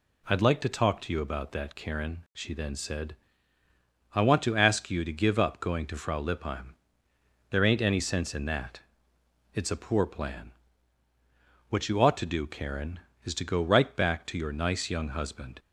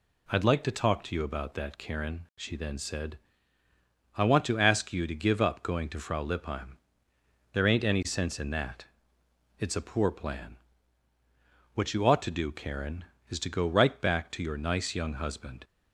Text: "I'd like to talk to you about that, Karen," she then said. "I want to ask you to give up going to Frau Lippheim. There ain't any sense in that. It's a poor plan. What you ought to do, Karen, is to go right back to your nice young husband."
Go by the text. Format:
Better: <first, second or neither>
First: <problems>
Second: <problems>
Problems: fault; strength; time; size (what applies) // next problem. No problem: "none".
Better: neither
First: none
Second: none